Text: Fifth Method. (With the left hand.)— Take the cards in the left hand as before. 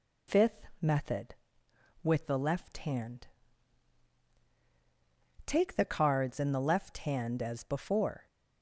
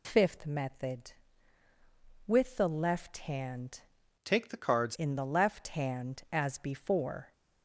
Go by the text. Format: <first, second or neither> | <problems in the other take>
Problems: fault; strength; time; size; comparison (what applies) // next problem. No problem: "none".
first | changes voice from "Take" to "cards"; from 4.2 to 4.9 s; 0.7 s long